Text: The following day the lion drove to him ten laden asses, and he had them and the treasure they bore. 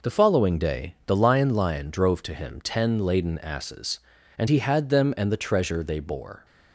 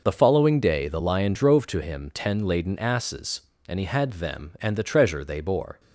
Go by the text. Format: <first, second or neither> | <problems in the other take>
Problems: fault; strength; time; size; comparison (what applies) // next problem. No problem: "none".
second | says "lion" twice; at 1.5 s